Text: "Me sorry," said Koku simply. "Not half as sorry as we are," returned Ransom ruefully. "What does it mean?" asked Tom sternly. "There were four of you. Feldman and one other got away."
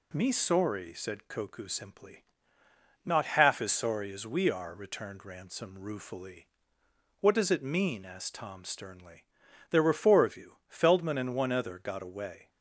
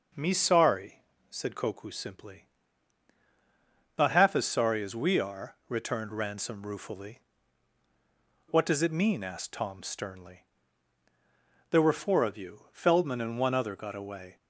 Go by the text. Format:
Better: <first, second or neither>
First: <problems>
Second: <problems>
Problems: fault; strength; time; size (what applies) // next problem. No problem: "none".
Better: neither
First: none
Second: none